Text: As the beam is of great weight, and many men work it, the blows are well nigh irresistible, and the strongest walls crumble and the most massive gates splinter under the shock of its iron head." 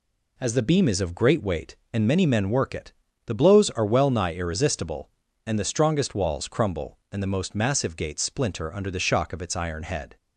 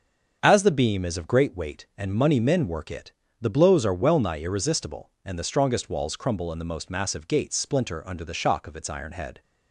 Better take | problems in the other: first | starts louder than the rest; until 1.4 s; 7 dB // says "money" for "many"; at 2.1 s

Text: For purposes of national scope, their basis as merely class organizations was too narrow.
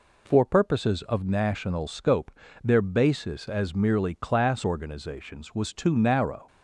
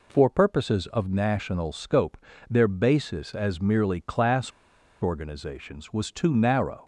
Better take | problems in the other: first | pauses between "class" and "organizations"; noticeable; at 4.5 s; 0.50 s long

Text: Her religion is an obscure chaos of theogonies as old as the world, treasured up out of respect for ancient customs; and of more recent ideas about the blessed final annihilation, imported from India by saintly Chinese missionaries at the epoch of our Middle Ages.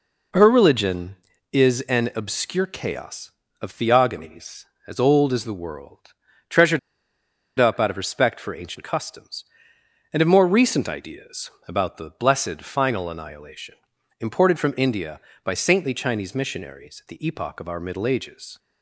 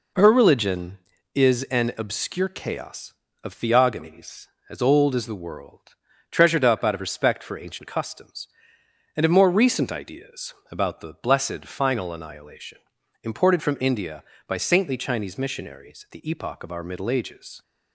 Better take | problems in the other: second | pauses between "treasured" and "up"; noticeable; at 6.7 s; 0.79 s long // pauses between "ideas" and "about"; slight; at 11.4 s; 0.18 s long; slight in the second

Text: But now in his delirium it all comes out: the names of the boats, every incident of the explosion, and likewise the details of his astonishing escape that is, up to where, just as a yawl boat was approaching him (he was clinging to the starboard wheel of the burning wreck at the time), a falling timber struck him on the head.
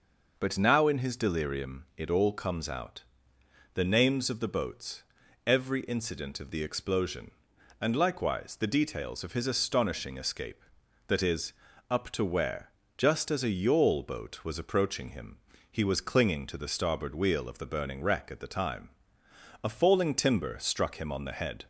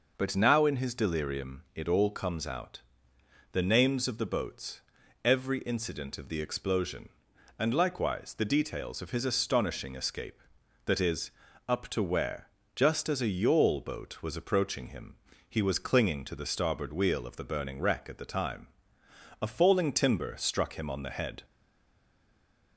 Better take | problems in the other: first | stays silent after the last word; noticeable; from 21.4 s on; 1.3 s long

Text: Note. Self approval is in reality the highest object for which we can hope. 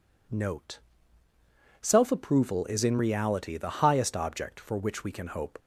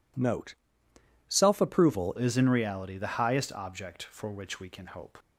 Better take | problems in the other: first | changes voice at "is"; from 2.1 s on; 3.0 s long

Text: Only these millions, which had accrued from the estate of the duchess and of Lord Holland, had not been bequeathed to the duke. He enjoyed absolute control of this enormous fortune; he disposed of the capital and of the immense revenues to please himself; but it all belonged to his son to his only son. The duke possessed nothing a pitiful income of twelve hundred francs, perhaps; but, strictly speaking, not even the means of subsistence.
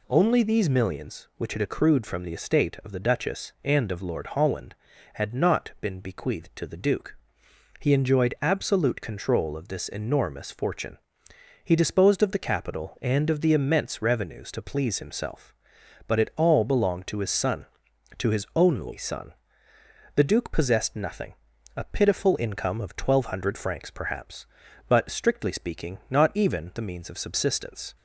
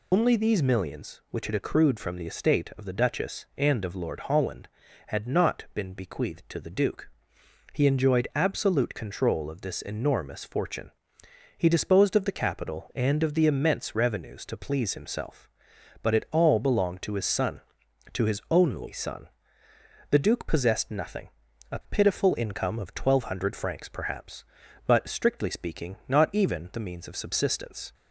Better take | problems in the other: first | loses the start of "Only"; at 0.1 s; 145 ms // pauses between "nothing" and "a"; at 21.3 s; 0.42 s long; also in the first

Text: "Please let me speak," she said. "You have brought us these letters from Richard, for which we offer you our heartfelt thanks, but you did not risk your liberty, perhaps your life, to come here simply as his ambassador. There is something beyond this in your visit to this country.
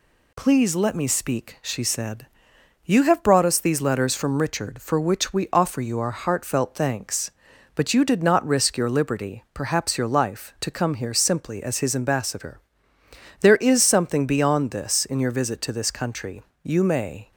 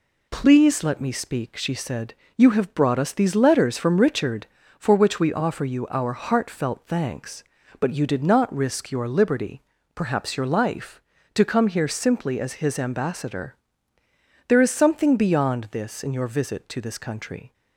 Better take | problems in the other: second | goes on to say "You may"; noticeable; from 16.6 s on; 0.68 s long

